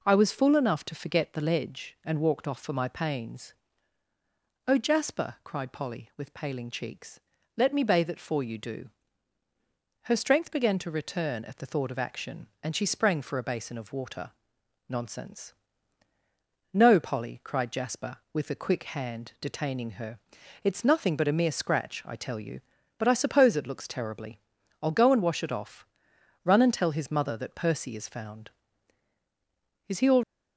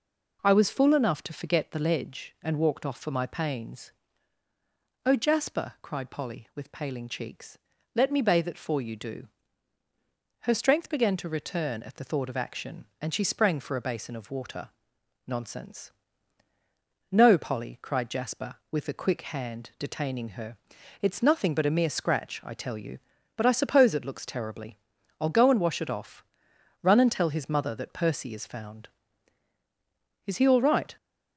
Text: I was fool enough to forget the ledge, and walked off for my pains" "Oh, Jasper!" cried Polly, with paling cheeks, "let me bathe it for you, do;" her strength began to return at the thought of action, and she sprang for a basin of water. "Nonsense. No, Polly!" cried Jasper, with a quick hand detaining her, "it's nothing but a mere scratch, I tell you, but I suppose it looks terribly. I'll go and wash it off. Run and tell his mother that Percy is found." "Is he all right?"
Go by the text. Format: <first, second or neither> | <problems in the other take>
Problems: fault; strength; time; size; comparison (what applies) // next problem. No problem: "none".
second | pauses between "pains" and "Oh"; at 3.5 s; 1.1 s long; also in the second // stops before "right"; at 30.2 s